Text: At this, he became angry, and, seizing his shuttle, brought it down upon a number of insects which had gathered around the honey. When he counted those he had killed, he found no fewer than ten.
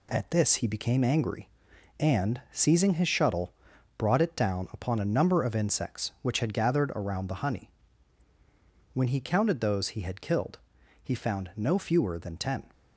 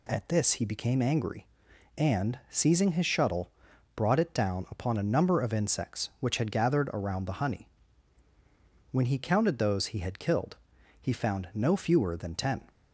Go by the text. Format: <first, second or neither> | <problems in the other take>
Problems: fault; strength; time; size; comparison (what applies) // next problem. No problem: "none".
second | gets quieter; noticeable; throughout; 5.5 dB